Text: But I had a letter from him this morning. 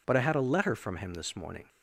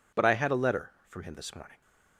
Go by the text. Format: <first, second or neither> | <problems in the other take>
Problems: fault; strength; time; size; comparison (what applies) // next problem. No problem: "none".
neither | none